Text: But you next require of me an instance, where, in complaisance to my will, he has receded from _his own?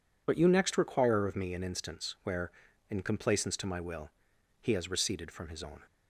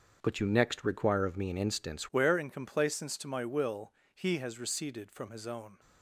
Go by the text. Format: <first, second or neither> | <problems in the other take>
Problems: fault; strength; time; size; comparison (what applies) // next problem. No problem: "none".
first | starts louder than the rest; until 1.2 s; 7 dB // changes voice at "where"; from 2.1 s on; 3.6 s long